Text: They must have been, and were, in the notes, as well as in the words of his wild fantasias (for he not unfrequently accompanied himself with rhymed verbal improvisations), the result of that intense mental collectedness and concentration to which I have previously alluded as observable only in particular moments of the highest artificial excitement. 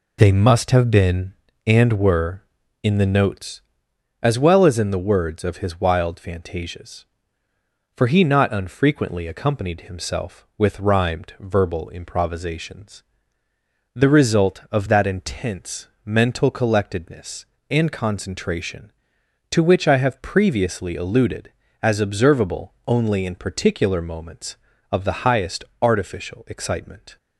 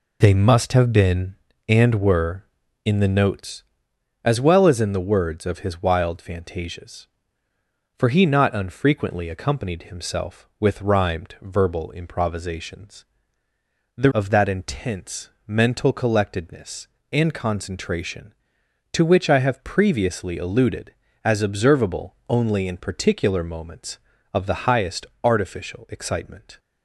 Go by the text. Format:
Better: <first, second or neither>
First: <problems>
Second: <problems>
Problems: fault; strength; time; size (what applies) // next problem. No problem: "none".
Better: first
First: pauses between "intense" and "mental"; slight; at 15.8 s; 0.18 s long // pauses between "observable" and "only"; slight; at 22.7 s; 0.16 s long // pauses between "highest" and "artificial"; slight; at 25.6 s; 0.18 s long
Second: skips "result"; at 14.1 s // pauses between "intense" and "mental"; slight; at 15.2 s; 0.18 s long // pauses between "observable" and "only"; slight; at 22.1 s; 0.16 s long // pauses between "highest" and "artificial"; slight; at 25.0 s; 0.18 s long